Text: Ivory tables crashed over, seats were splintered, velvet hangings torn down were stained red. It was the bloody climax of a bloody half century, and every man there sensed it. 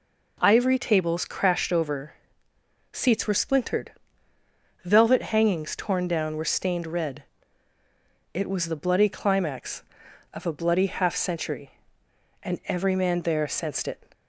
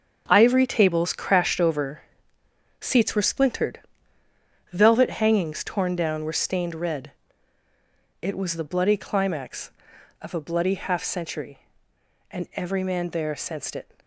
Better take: first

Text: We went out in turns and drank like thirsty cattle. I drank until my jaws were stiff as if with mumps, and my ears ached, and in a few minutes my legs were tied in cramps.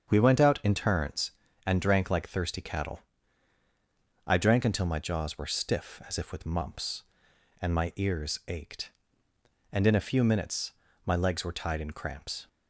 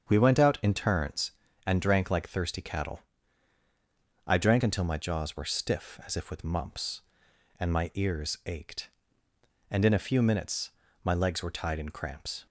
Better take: neither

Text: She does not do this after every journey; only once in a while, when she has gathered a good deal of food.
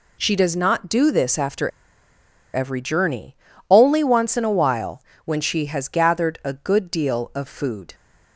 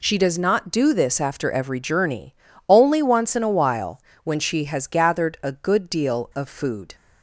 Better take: second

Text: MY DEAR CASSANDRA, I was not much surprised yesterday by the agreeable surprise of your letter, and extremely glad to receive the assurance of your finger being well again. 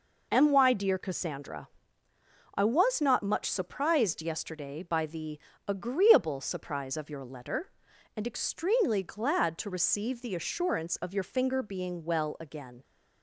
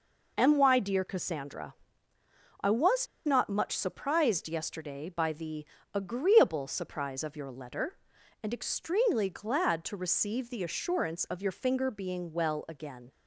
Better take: first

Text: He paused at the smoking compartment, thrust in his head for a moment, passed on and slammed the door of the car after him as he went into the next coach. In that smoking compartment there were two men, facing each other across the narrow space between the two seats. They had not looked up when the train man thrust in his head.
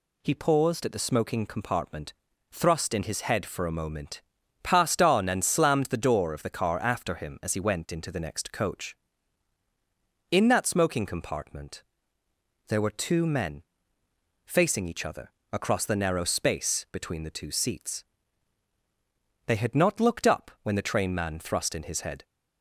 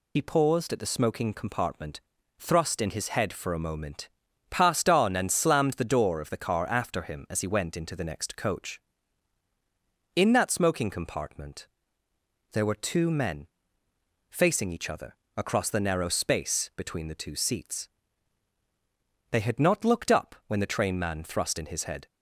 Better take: first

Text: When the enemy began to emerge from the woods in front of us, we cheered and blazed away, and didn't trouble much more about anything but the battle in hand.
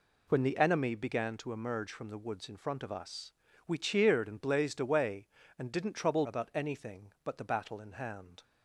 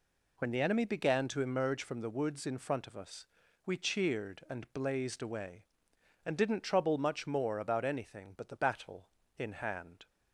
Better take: second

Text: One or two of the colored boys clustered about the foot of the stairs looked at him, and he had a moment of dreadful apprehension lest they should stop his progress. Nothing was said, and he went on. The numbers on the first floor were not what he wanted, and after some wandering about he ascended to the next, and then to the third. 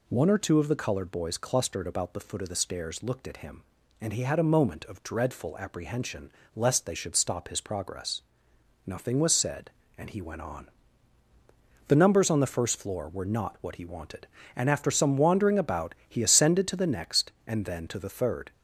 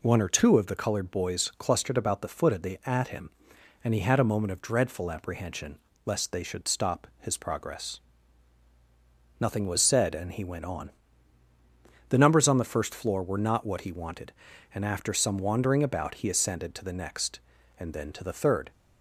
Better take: first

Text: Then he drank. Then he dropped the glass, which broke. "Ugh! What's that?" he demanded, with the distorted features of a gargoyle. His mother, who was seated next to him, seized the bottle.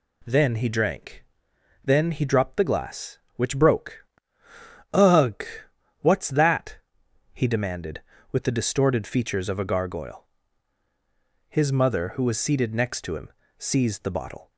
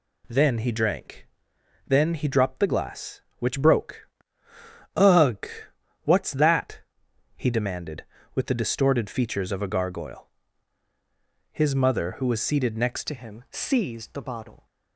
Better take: first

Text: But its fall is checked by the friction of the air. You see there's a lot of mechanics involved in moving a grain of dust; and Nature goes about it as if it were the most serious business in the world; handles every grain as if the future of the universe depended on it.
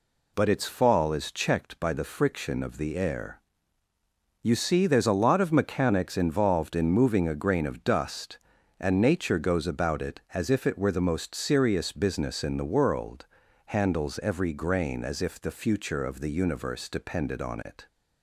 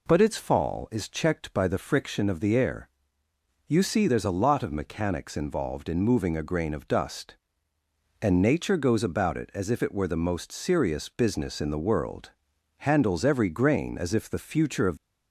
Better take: first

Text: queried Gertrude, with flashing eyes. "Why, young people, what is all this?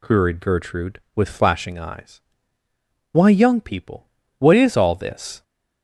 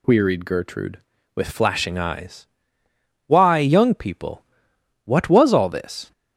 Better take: first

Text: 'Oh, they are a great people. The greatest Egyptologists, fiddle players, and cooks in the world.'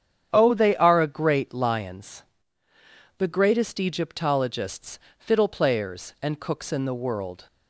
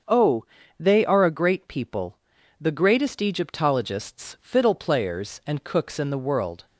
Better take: second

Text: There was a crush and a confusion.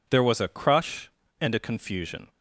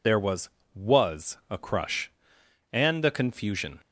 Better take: first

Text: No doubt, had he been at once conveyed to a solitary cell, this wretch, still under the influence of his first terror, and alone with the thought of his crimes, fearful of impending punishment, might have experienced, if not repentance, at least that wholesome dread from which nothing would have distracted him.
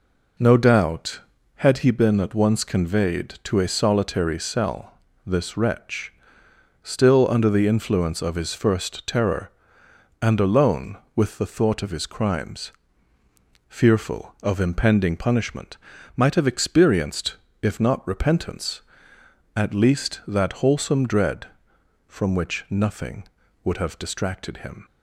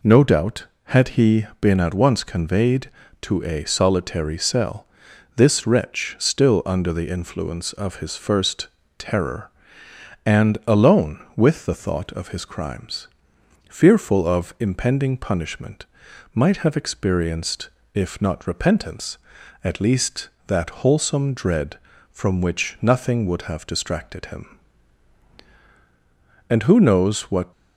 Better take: first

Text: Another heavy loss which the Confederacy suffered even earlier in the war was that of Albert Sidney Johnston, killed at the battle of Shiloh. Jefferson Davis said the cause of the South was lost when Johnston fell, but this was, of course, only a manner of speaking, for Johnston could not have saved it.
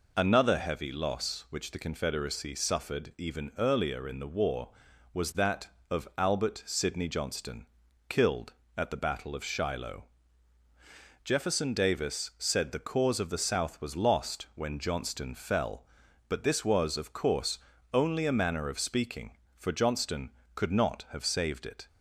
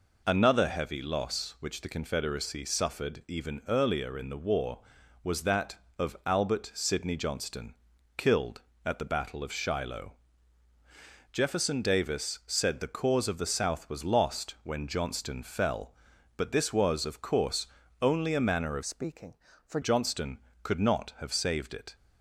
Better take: first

